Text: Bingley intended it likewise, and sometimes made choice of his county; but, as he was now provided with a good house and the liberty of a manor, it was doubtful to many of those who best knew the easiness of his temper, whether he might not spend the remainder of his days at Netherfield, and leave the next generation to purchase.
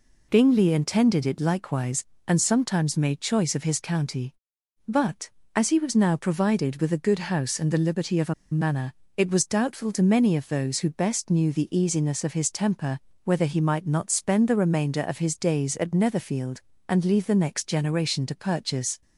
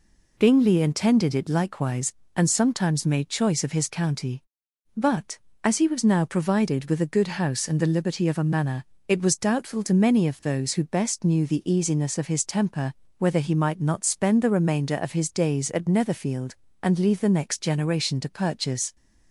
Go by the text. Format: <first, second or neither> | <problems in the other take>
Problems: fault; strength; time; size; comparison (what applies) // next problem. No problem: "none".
second | pauses between "a" and "manor"; slight; at 8.3 s; 0.19 s long